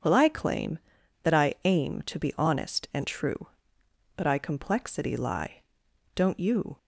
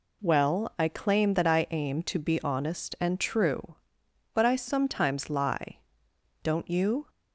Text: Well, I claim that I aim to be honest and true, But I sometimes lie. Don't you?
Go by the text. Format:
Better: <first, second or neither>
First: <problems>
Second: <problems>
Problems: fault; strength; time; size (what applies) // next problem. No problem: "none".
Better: second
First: says "complexity" for "sometimes"; at 4.3 s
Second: none